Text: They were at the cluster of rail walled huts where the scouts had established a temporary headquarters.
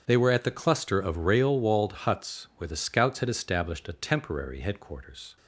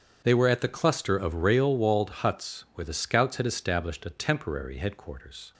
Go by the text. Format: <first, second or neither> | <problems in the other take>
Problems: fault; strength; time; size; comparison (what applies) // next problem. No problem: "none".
neither | starts louder than the rest; strong; the same in both